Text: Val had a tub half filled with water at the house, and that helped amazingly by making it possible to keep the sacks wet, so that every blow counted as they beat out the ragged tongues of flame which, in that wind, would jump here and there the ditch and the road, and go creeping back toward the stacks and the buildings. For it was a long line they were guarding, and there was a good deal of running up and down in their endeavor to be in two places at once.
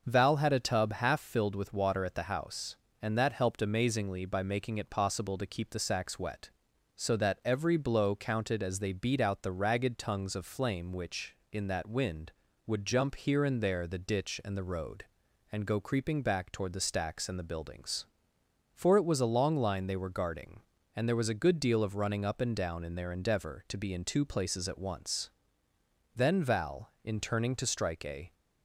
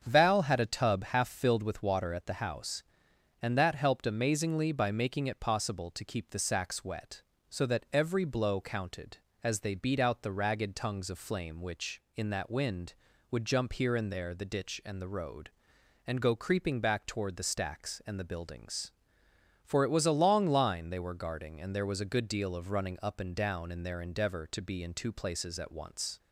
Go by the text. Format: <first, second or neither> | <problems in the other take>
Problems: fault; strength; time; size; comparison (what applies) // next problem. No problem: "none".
second | starts louder than the rest; until 1.1 s; 6.5 dB; strong in the second // goes on to say "Then Val in turning to strike a"; strong; from 26.1 s on; 2.1 s long